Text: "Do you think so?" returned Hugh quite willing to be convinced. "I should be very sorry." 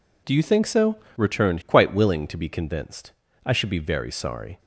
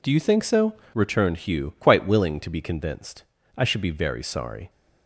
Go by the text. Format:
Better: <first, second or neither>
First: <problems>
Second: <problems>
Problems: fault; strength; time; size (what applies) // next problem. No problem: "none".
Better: second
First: skips "Hugh"; at 1.6 s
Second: none